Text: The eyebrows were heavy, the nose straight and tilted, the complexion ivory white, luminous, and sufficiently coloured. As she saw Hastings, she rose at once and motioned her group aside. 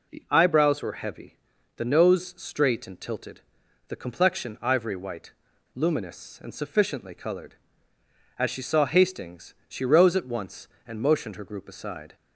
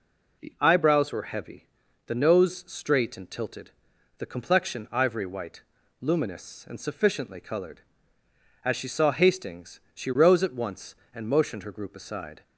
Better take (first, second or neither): neither